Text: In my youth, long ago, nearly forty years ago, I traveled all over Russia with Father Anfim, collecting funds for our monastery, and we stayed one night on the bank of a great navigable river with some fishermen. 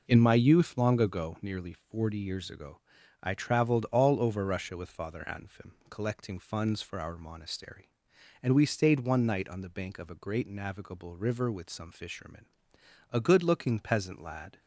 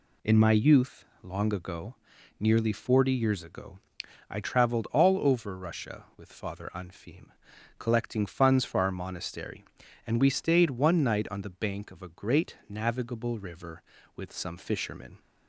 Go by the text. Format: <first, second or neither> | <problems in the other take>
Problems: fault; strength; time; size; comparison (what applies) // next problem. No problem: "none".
second | goes on to say "A good looking peasant lad"; from 13.1 s on; 1.4 s long